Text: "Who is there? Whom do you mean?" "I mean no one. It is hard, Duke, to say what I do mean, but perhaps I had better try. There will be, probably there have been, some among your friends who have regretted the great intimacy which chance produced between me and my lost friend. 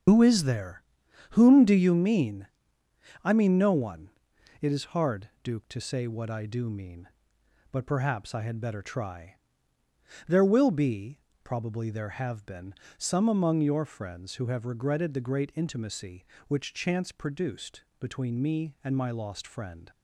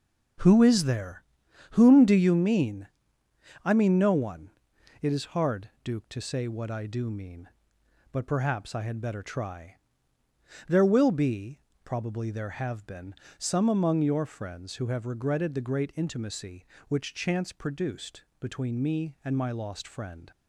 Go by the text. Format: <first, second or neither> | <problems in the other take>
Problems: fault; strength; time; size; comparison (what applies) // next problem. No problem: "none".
second | loses the start of "Who"; at 0.0 s; 105 ms // starts louder than the rest; until 1.5 s; 7 dB // pauses between "produced" and "between"; slight; at 17.8 s; 0.16 s long; slight in the second